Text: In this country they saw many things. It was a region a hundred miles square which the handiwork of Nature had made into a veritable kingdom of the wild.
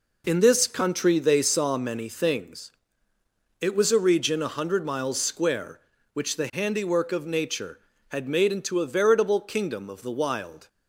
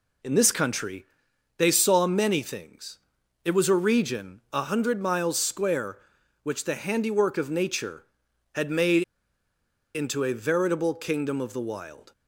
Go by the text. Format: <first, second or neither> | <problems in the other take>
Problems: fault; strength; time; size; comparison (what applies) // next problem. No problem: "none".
first | pauses between "country" and "they"; noticeable; at 1.0 s; 0.52 s long // pauses between "made" and "into"; noticeable; at 9.0 s; 0.93 s long